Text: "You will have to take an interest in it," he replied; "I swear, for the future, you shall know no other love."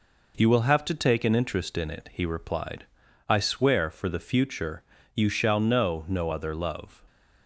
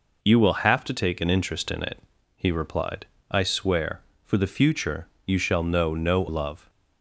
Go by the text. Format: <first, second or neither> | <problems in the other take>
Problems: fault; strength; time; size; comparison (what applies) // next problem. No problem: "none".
first | skips "other"; at 6.2 s